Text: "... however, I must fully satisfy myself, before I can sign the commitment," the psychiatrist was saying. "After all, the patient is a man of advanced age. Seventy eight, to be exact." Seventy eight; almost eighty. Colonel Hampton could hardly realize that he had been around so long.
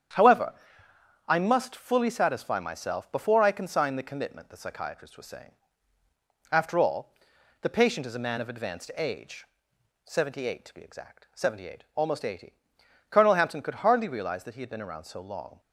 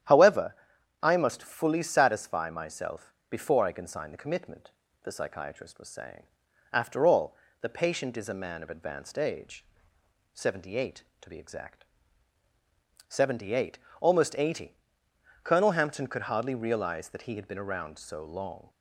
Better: neither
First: starts louder than the rest; strong; until 1.8 s; 9 dB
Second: starts louder than the rest; strong; until 1.5 s; 10.5 dB

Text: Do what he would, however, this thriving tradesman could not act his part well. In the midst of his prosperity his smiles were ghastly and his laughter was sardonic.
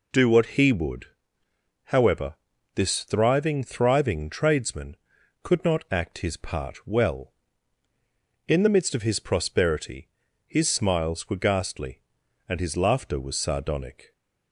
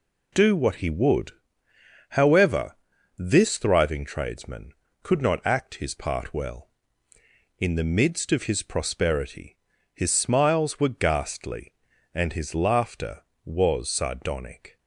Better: second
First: says "thriving" twice; at 3.6 s // pauses between "prosperity" and "his"; at 10.0 s; 0.38 s long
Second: pauses between "prosperity" and "his"; slight; at 9.5 s; 0.36 s long

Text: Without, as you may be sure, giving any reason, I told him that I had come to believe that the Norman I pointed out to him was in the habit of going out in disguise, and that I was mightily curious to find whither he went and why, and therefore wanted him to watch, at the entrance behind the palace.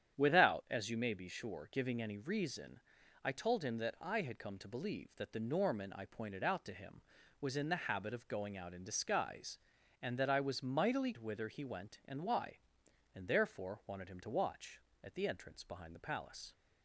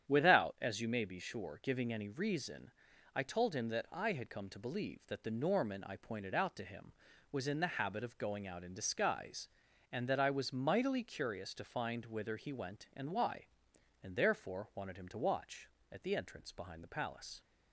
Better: second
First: starts louder than the rest; strong; until 1.2 s; 9 dB // skips "curious to find"; at 11.1 s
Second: starts louder than the rest; strong; until 1.1 s; 9 dB

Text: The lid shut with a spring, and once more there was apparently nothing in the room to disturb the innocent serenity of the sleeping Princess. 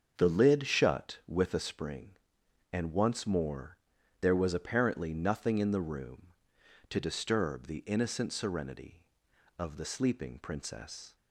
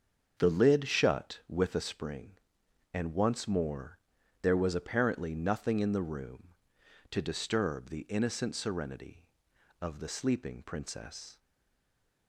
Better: first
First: starts louder than the rest; until 1.1 s; 7 dB // pauses between "more" and "there"; at 3.7 s; 0.44 s long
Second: starts louder than the rest; until 1.3 s; 7 dB // pauses between "more" and "there"; at 3.9 s; 0.44 s long // stays silent after the last word; slight; from 11.3 s on; 0.9 s long

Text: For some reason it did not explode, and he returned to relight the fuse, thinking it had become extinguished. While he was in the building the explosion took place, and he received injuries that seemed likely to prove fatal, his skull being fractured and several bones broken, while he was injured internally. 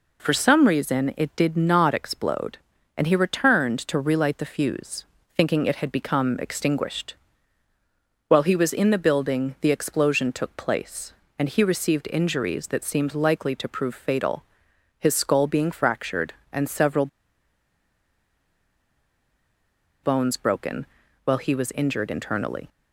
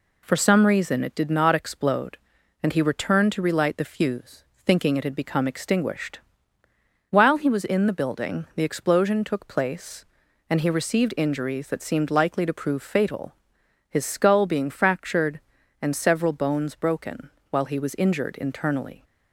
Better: second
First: pauses between "several" and "bones"; strong; at 17.0 s; 2.9 s long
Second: none

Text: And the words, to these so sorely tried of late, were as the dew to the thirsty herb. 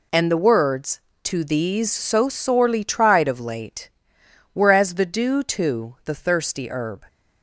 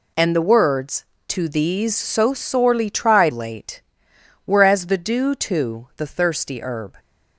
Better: first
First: none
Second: skips "of"; at 3.3 s

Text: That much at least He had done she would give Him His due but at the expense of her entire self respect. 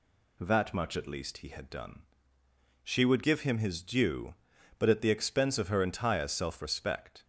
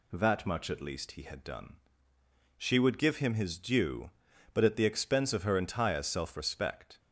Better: neither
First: pauses between "done" and "she"; noticeable; at 2.0 s; 0.82 s long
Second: pauses between "done" and "she"; noticeable; at 1.7 s; 0.82 s long

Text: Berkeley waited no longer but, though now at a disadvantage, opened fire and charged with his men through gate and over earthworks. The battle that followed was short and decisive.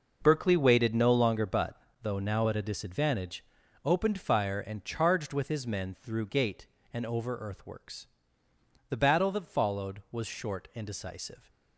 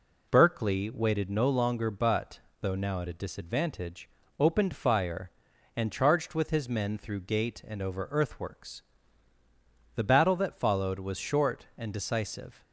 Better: neither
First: none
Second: none

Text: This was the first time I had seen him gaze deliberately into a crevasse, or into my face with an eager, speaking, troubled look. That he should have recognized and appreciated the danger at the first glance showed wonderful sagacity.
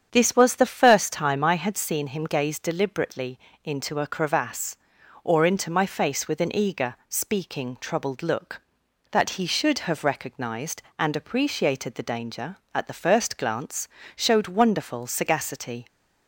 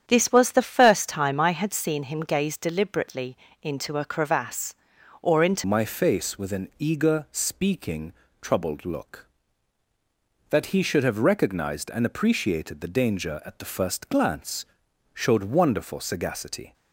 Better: first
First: starts louder than the rest; strong; until 1.1 s; 8 dB // pauses between "deliberately" and "into"; slight; at 3.4 s; 0.24 s long // pauses between "glance" and "showed"; slight; at 13.8 s; 0.26 s long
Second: starts louder than the rest; strong; until 1.0 s; 9 dB // pauses between "deliberately" and "into"; slight; at 3.3 s; 0.24 s long // changes voice at "my"; from 5.6 s on; 11.1 s long // pauses between "glance" and "showed"; noticeable; at 14.6 s; 0.48 s long

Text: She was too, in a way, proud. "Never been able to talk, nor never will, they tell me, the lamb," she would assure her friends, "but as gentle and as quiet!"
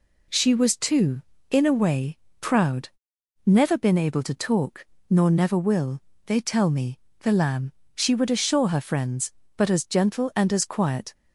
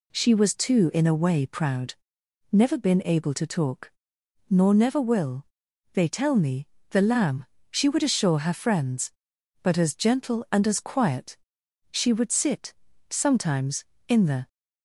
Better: first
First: none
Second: goes on to say "She would sit sometimes in the"; strong; from 11.9 s on; 2.5 s long

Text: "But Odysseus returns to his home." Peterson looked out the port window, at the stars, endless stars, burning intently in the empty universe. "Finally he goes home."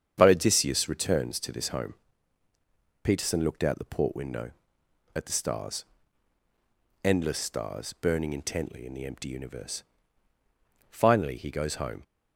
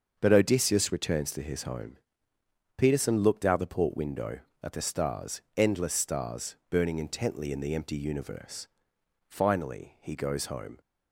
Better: second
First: starts louder than the rest; strong; until 1.1 s; 8 dB // says "this" for "his"; at 1.5 s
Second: starts louder than the rest; until 1.2 s; 6.5 dB

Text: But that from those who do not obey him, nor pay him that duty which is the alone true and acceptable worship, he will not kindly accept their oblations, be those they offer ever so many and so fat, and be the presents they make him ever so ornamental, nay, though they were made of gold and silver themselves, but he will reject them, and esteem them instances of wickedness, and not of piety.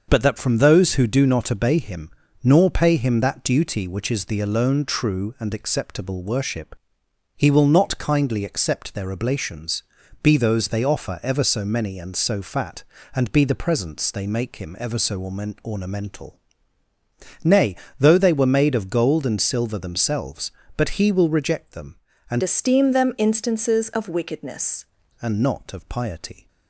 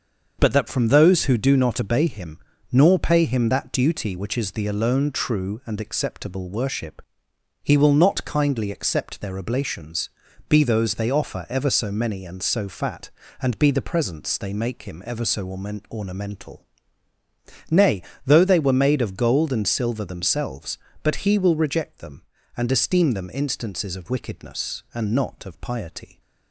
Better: second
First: starts louder than the rest; until 1.1 s; 6.5 dB // pauses between "so" and "ornamental"; at 15.2 s; 0.42 s long // changes voice from "esteem" to "wickedness"; from 22.4 to 24.8 s; 2.4 s long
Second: starts louder than the rest; until 1.4 s; 6.5 dB // pauses between "so" and "ornamental"; at 15.4 s; 0.42 s long

